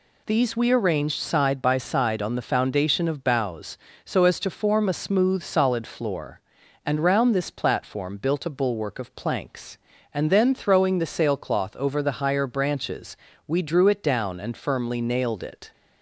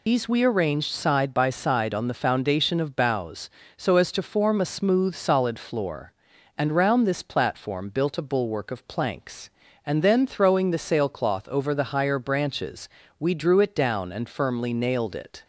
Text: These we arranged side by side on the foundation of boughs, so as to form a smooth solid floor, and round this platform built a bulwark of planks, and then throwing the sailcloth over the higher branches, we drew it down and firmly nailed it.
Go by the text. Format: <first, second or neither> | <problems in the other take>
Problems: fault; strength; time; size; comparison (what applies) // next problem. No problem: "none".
first | loses the start of "These"; at 0.0 s; 85 ms